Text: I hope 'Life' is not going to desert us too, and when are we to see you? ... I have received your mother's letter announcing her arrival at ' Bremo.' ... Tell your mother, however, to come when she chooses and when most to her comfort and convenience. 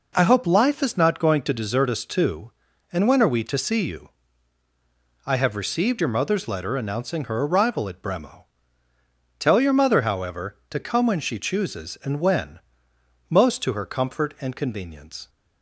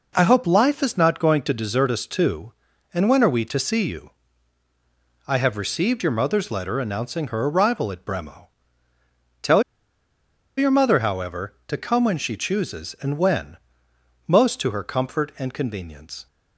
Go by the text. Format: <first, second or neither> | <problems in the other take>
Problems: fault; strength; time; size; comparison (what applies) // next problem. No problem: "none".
first | pauses between "Tell" and "your"; noticeable; at 9.6 s; 0.95 s long // pauses between "when" and "most"; noticeable; at 13.5 s; 0.74 s long; noticeable in the first